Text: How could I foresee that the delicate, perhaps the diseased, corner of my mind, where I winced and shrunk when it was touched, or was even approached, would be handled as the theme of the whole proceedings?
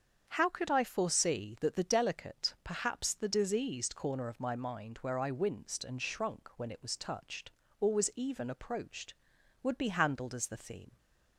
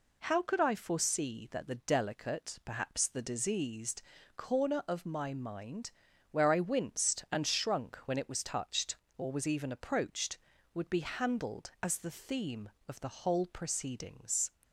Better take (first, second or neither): second